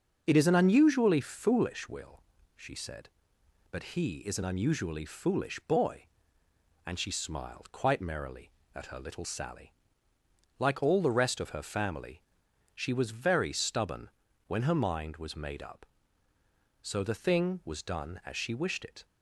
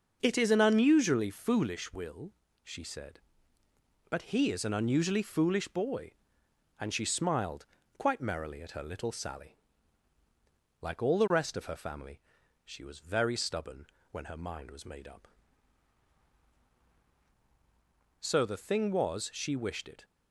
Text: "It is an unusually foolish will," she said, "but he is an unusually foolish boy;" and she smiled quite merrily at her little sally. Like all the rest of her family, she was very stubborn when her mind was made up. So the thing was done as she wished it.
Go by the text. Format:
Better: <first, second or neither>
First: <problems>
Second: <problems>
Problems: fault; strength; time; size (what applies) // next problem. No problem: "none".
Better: first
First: starts louder than the rest; until 1.2 s; 6.5 dB // pauses between "stubborn" and "when"; slight; at 14.1 s; 0.34 s long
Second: starts louder than the rest; noticeable; until 1.2 s; 6 dB // pauses between "smiled" and "quite"; slight; at 7.6 s; 0.30 s long // pauses between "stubborn" and "when"; slight; at 13.8 s; 0.24 s long // skips "done as"; at 19.3 s